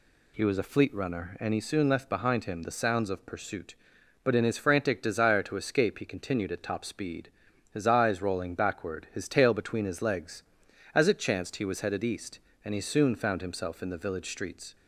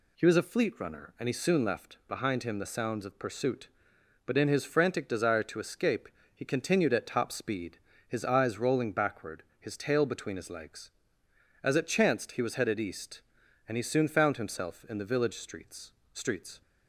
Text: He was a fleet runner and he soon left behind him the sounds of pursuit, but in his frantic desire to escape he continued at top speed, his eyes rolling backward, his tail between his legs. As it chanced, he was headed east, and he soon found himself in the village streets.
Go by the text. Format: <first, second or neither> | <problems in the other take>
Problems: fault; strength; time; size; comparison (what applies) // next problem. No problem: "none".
first | pauses between "escape" and "he"; slight; at 6.0 s; 0.26 s long // says "streets" twice; at 16.1 s